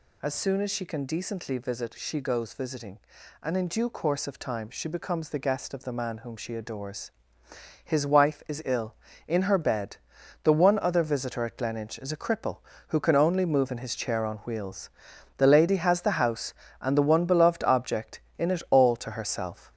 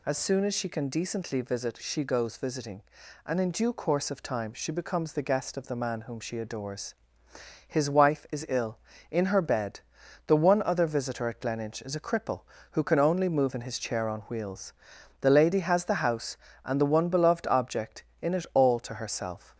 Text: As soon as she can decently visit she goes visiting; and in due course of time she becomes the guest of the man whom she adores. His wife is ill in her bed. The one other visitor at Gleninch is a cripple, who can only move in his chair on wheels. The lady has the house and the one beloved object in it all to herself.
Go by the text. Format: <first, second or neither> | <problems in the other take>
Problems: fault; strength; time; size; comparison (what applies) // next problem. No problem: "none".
second | gets louder; noticeable; throughout; 5.5 dB